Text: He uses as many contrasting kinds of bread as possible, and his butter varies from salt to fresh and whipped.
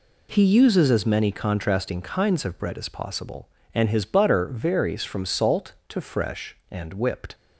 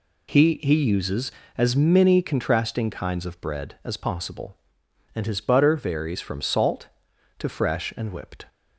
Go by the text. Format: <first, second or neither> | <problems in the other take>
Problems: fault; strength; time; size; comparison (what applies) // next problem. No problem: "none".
first | says "He" twice; at 0.6 s